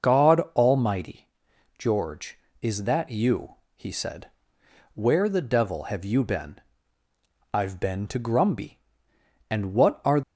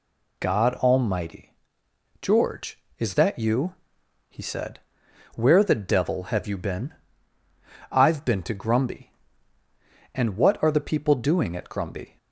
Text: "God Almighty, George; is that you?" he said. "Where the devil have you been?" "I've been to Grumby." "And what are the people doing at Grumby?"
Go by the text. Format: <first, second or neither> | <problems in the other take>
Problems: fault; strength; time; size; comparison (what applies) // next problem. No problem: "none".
second | pauses between "God" and "Almighty"; slight; at 0.4 s; 0.16 s long // stops before "the people doing at Grumby"; at 10.2 s